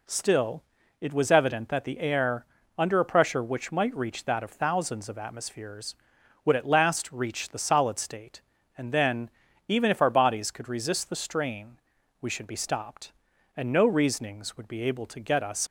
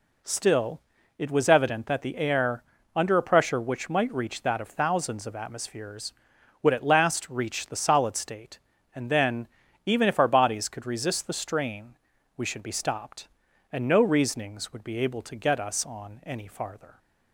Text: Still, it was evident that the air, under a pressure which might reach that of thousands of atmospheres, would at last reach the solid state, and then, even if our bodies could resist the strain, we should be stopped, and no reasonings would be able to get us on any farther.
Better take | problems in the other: second | stops before "on any farther"; at 15.6 s

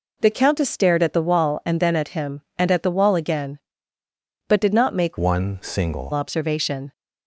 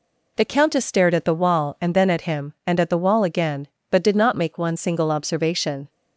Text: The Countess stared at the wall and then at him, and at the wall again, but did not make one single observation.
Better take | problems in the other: second | changes voice from "one" to "single"; from 5.1 to 6.1 s; 1.0 s long

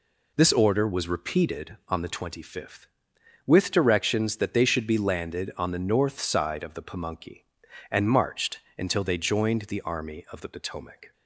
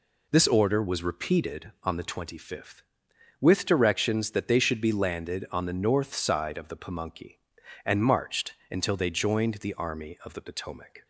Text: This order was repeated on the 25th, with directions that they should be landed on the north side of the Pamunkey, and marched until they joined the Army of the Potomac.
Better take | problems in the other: neither | pauses between "marched" and "until"; slight; the same in both

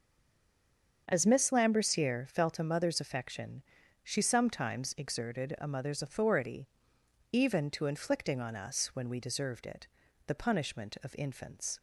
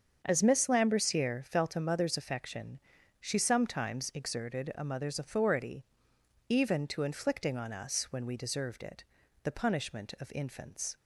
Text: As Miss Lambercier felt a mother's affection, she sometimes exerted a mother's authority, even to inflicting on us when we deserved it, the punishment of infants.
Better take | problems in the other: second | stays silent before the first word; until 1.0 s; 1.0 s long // starts louder than the rest; until 2.1 s; 7 dB; also in the second

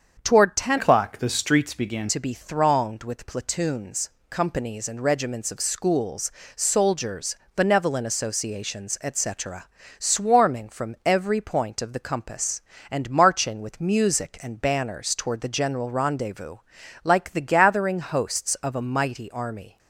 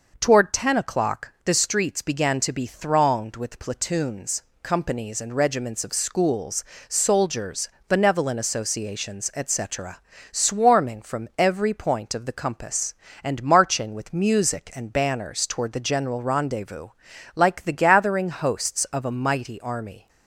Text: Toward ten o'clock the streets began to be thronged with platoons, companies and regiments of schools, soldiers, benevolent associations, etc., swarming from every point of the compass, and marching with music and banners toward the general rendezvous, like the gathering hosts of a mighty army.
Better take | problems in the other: second | starts louder than the rest; strong; until 1.2 s; 7 dB // changes voice from "o'clock" to "began"; from 0.7 to 2.0 s; 1.3 s long

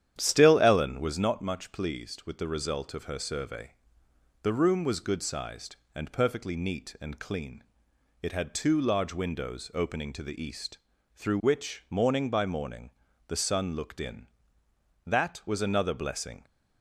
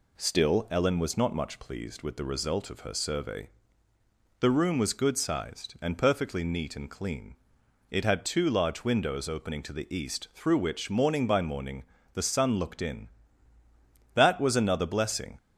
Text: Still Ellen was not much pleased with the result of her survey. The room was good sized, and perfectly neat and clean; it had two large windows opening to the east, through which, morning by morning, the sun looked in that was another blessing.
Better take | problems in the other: second | starts louder than the rest; strong; until 1.4 s; 10 dB

